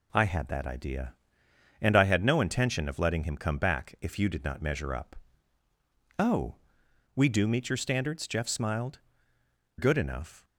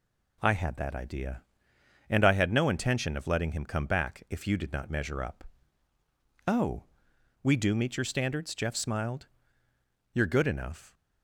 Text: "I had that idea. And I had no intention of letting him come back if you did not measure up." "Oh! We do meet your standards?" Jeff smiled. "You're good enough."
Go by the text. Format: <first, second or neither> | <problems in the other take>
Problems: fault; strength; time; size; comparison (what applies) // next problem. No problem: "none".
second | skips "You're"; at 9.3 s